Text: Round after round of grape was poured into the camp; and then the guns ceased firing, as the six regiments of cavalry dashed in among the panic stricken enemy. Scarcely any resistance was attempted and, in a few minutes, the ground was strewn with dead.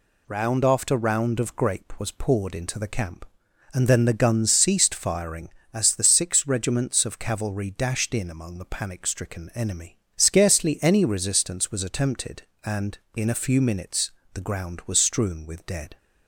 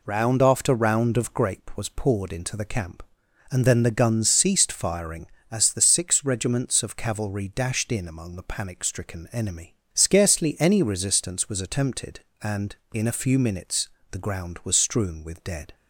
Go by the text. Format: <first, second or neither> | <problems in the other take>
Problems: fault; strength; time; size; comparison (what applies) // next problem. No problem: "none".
first | starts louder than the rest; slight; until 1.5 s; 3 dB